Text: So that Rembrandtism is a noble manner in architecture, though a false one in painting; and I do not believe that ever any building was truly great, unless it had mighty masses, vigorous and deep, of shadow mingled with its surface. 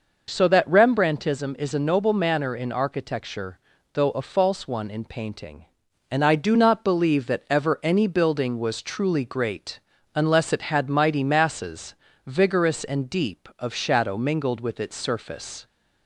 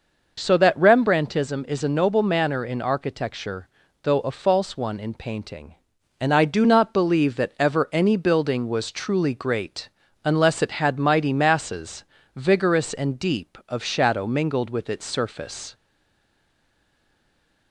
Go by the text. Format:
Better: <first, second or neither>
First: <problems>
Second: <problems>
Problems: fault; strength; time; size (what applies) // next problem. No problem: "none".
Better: first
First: none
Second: stays silent after the last word; noticeable; from 15.7 s on; 2.0 s long